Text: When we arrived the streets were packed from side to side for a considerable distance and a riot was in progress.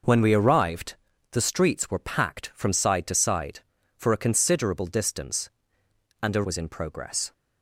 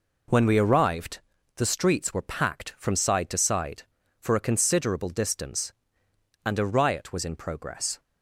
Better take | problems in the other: second | pauses between "arrived" and "the"; slight; at 0.9 s; 0.36 s long; slight in the second // skips "riot"; at 6.4 s

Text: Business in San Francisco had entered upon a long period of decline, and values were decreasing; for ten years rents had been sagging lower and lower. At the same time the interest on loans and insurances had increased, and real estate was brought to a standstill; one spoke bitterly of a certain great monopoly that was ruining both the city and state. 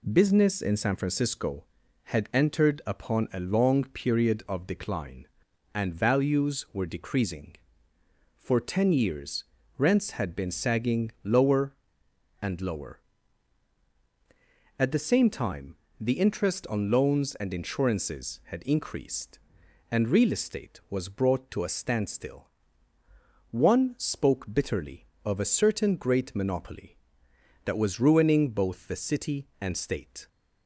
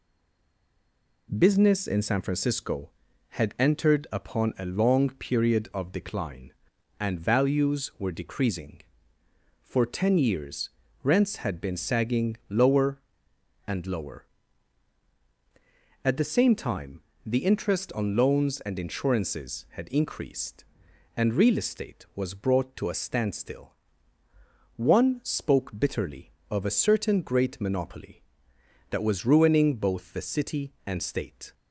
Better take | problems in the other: first | stays silent before the first word; noticeable; until 1.2 s; 1.2 s long // pauses between "years" and "rents"; slight; at 10.7 s; 0.32 s long; slight in the first // pauses between "time" and "the"; slight; at 17.0 s; 0.26 s long; slight in the first

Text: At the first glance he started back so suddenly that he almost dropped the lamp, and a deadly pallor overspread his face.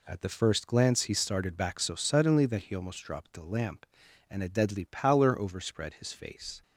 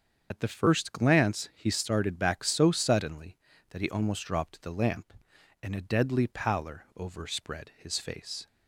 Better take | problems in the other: first | loses the start of "At"; at 0.3 s; 50 ms // starts louder than the rest; until 1.3 s; 7 dB

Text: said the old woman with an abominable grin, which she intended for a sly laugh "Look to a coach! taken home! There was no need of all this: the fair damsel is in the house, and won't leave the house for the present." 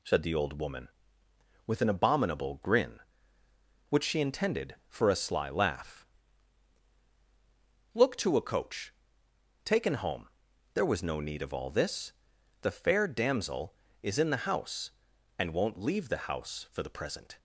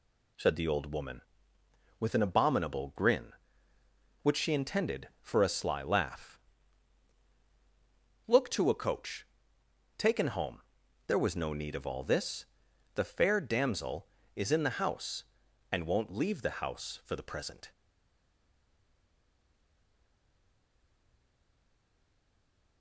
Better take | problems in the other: first | pauses between "laugh" and "Look"; strong; at 6.4 s; 1.8 s long; strong in the first // stays silent after the last word; strong; from 17.7 s on; 5.1 s long

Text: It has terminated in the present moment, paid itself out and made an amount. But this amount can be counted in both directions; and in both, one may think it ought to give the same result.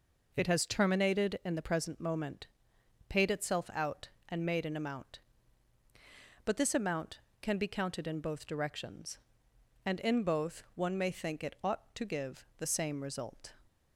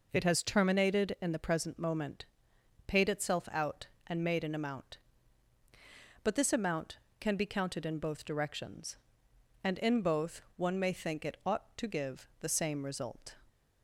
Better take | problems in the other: neither | none

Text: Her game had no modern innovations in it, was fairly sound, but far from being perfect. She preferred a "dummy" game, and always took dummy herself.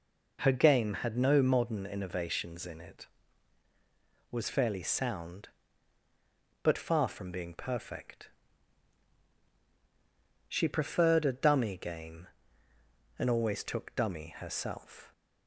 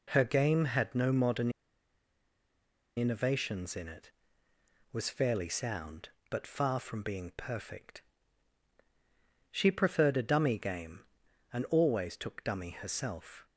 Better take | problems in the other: first | pauses between "modern" and "innovations"; strong; at 1.5 s; 1.4 s long

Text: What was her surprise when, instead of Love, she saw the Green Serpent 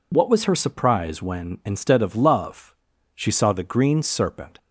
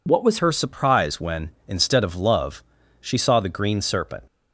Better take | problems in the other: first | changes voice at "her"; from 0.3 s on; 3.9 s long

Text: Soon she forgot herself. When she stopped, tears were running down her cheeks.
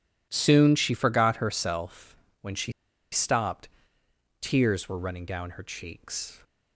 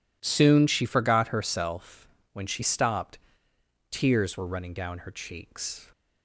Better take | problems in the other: second | pauses between "she" and "stopped"; at 2.7 s; 0.40 s long

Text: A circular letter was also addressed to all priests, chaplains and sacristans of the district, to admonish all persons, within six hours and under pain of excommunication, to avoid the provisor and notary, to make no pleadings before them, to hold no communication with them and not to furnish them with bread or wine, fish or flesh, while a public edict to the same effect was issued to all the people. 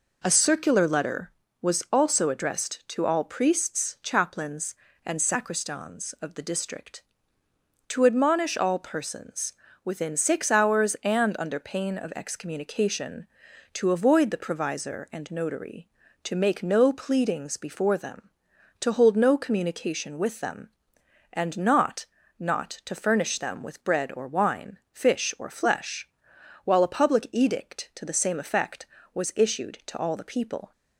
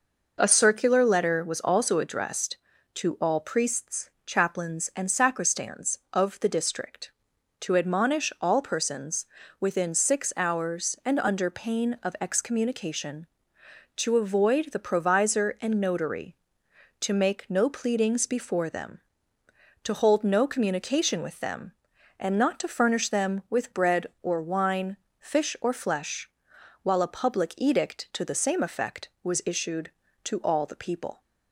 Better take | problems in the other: second | says "not" twice; at 22.3 s

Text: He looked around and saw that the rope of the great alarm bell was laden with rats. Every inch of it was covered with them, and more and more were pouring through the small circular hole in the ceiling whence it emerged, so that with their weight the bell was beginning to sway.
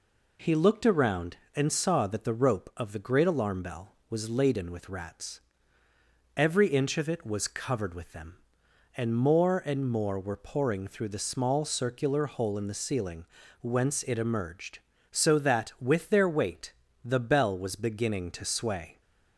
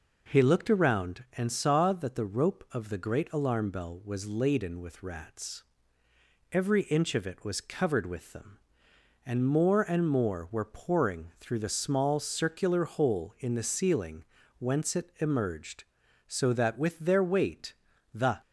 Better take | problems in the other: first | pauses between "ceiling" and "whence"; slight; at 14.2 s; 0.34 s long; slight in the first // pauses between "weight" and "the"; at 17.7 s; 0.38 s long; slight in the first // stops before "bell was beginning to sway"; at 18.4 s

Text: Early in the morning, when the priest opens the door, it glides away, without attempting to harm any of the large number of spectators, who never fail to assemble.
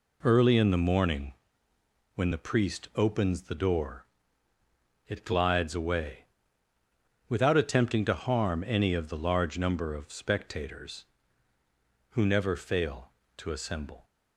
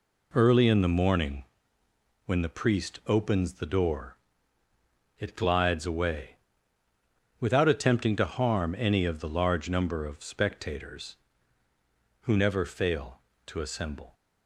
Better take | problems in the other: neither | none

